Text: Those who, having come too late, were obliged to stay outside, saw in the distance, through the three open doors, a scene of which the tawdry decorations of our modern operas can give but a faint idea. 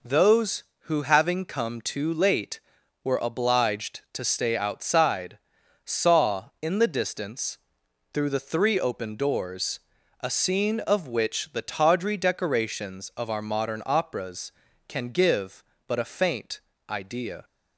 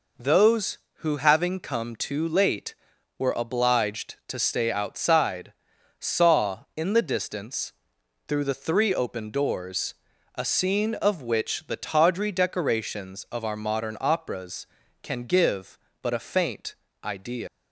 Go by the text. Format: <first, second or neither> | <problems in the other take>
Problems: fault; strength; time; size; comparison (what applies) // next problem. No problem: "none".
first | pauses between "faint" and "idea"; slight; at 16.7 s; 0.28 s long; slight in the first // leaves "idea" unfinished; at 17.4 s; 110 ms